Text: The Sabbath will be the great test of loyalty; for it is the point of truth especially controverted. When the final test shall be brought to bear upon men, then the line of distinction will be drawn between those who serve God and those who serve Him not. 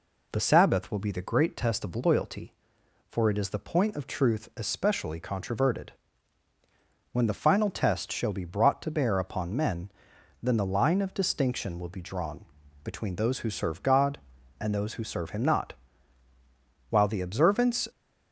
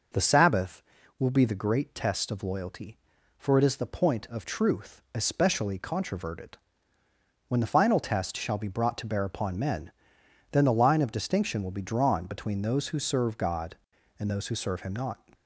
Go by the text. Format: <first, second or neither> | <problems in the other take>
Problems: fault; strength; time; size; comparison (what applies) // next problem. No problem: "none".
second | pauses between "drawn" and "between"; at 12.4 s; 0.38 s long // goes on to say "While the observance"; noticeable; from 16.8 s on; 0.98 s long